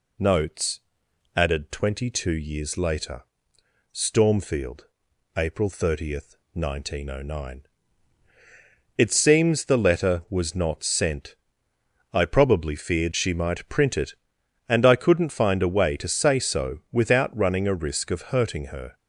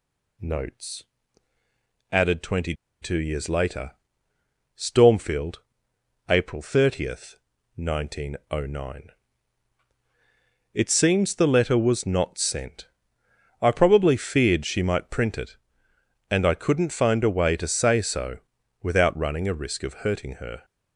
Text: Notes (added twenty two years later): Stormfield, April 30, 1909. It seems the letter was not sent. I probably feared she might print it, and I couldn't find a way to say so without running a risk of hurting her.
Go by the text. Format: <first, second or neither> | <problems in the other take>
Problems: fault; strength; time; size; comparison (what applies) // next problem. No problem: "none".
first | pauses between "twenty" and "two"; slight; at 2.7 s; 0.28 s long // pauses between "so" and "without"; at 18.3 s; 0.42 s long